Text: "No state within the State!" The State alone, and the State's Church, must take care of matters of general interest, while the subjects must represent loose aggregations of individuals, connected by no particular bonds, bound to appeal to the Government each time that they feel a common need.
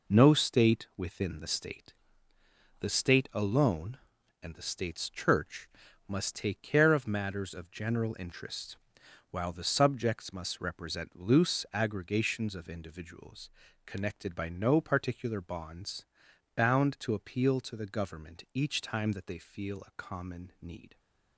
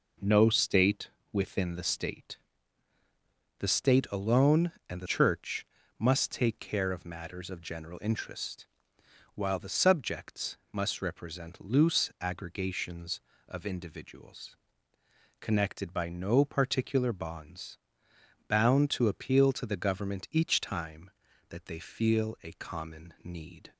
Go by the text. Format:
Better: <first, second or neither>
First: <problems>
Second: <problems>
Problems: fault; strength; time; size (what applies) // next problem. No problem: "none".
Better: first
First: none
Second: pauses between "state" and "within"; slight; at 1.1 s; 0.20 s long // skips "State's"; at 5.0 s // pauses between "subjects" and "must"; slight; at 10.5 s; 0.16 s long